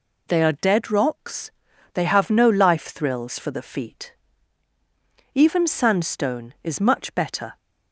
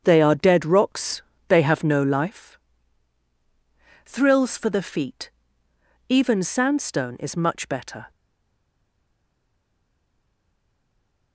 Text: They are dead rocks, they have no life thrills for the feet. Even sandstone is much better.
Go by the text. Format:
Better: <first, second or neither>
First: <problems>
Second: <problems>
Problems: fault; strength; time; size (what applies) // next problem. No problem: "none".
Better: first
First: none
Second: starts louder than the rest; strong; until 1.0 s; 7.5 dB // pauses between "life" and "thrills"; strong; at 2.5 s; 1.5 s long // stays silent after the last word; strong; from 8.1 s on; 3.2 s long